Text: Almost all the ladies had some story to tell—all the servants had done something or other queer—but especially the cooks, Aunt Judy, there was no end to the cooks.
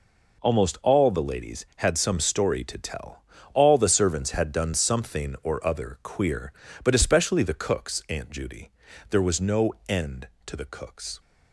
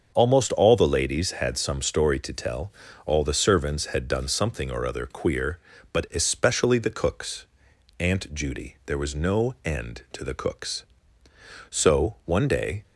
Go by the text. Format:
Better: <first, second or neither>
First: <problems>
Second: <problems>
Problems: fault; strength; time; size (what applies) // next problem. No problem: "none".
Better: first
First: none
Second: starts louder than the rest; until 1.1 s; 6.5 dB // goes on to say "So one day"; noticeable; from 11.6 s on; 1.1 s long